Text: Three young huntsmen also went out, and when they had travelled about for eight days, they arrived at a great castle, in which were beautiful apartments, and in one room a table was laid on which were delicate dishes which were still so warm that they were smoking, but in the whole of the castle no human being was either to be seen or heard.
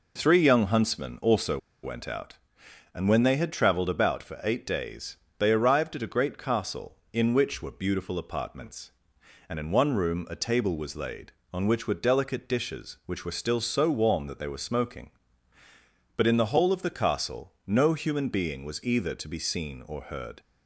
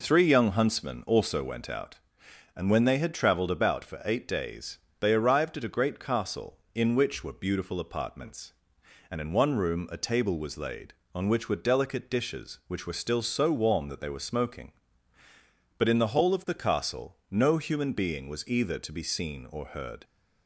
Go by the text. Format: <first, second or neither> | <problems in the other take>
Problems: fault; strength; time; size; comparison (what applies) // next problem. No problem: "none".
second | pauses between "also" and "went"; slight; at 1.5 s; 0.24 s long